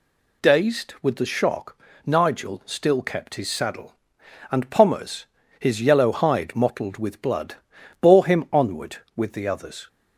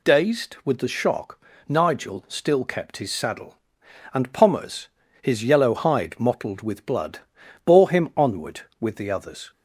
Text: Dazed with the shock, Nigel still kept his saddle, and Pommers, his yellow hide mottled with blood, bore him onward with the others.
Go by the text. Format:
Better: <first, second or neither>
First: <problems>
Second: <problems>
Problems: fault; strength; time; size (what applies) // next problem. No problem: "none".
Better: neither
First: none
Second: none